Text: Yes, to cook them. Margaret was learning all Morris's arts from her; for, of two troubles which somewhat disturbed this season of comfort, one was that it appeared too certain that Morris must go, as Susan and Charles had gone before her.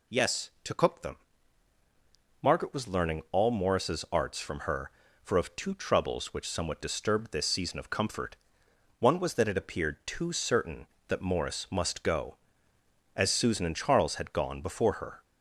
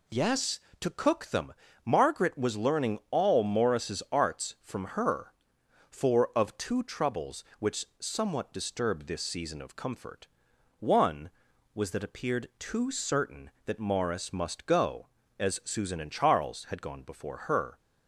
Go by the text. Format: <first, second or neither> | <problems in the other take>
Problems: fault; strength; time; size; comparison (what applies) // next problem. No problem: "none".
first | skips "it"; at 12.0 s